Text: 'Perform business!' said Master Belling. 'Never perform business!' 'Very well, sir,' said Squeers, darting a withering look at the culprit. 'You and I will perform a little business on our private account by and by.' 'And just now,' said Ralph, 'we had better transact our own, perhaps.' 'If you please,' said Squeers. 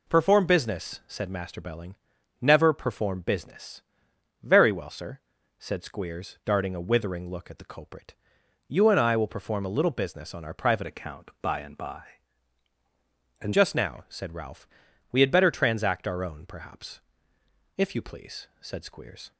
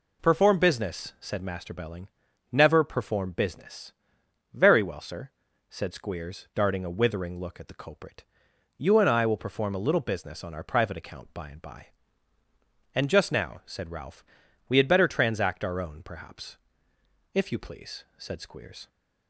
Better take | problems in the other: second | changes voice from "account" to "And"; from 10.8 to 13.5 s; 2.7 s long

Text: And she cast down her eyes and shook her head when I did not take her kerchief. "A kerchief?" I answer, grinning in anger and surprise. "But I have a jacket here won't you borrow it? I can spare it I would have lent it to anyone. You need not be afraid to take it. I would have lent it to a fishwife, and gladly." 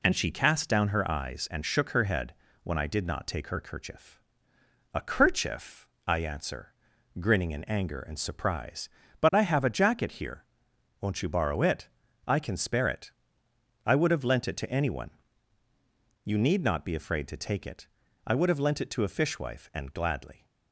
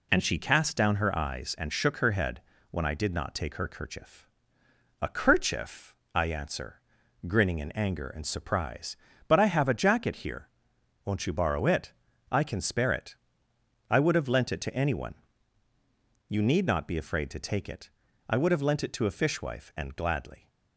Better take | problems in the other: neither | pauses between "head" and "when"; slight; the same in both // pauses between "here" and "won't"; noticeable; the same in both // pauses between "it" and "I"; noticeable; the same in both

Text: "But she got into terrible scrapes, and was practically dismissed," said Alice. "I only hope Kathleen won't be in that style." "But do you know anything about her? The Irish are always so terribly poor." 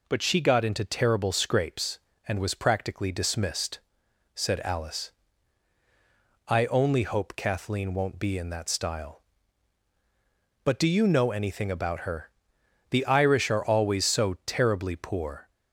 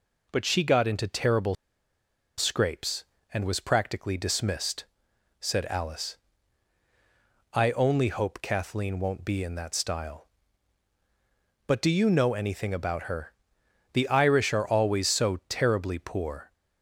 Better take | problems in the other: first | pauses between "terrible" and "scrapes"; noticeable; at 1.5 s; 0.83 s long

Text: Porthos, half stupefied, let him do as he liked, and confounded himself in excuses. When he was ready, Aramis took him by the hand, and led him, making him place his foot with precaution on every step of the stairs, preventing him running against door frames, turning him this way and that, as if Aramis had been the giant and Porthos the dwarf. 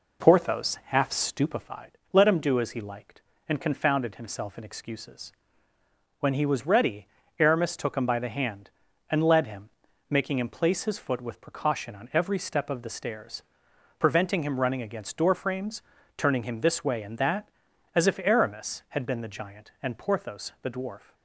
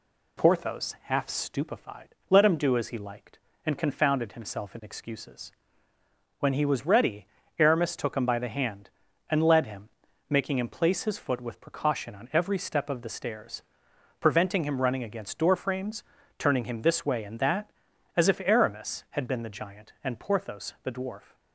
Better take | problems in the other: second | starts louder than the rest; noticeable; until 1.9 s; 4 dB

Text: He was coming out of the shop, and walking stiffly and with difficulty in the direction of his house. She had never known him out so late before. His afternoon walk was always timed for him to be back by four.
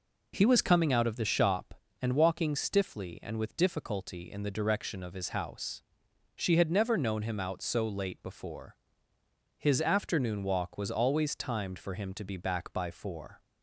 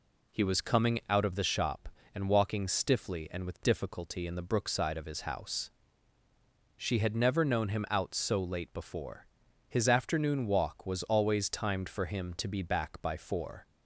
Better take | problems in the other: first | says "brookside" for "direction"; at 4.4 s

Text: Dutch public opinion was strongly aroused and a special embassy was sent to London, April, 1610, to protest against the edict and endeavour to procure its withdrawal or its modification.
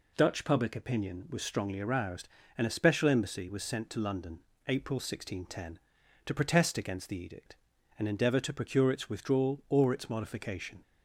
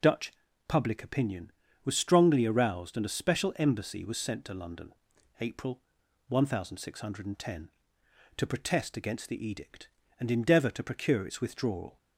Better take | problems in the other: first | pauses between "Dutch" and "public"; slight; at 0.3 s; 0.36 s long // stops before "or its modification"; at 11.9 s

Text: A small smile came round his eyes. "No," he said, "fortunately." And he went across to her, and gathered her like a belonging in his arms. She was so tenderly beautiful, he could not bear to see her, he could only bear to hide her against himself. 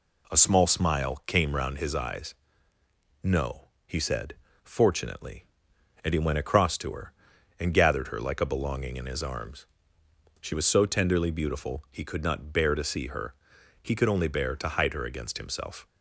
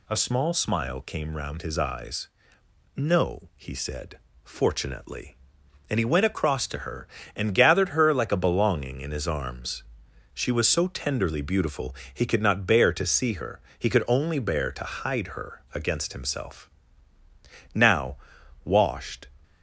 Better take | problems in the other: first | goes on to say "Now washed"; from 17.7 s on; 1.5 s long

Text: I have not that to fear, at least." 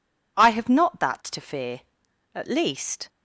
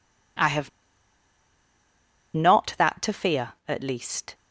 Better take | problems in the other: first | pauses between "have" and "not"; strong; at 0.6 s; 1.6 s long

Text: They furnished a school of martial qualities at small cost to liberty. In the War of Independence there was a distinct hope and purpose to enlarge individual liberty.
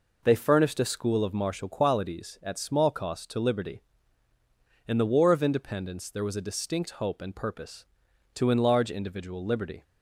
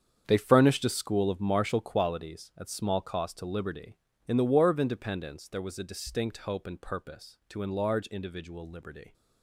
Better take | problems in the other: first | gets quieter; strong; throughout; 13 dB

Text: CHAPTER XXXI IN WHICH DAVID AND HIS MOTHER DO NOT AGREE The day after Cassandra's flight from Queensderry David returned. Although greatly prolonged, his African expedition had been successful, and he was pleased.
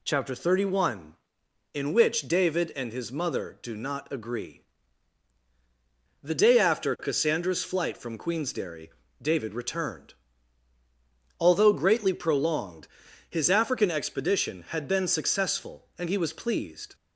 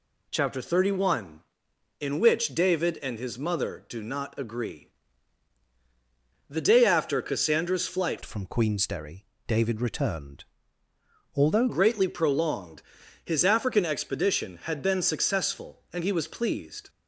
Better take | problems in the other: first | pauses between "AGREE" and "The"; strong; at 4.8 s; 1.6 s long; strong in the first // changes voice from "from" to "Although"; from 8.2 to 11.6 s; 3.4 s long // pauses between "Queensderry" and "David"; slight; at 9.2 s; 0.20 s long; slight in the first

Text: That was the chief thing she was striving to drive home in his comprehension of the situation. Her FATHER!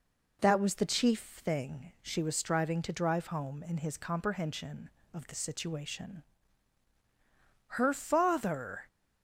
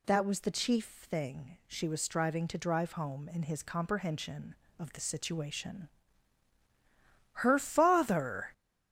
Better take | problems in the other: first | gets louder; throughout; 6.5 dB

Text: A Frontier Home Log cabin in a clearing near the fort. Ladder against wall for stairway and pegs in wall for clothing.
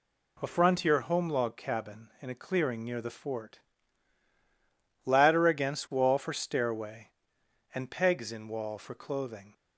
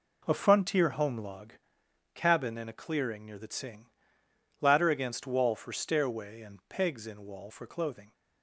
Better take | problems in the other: first | pauses between "Log" and "cabin"; noticeable; at 1.5 s; 0.62 s long // says "tsing" for "fort"; at 3.4 s

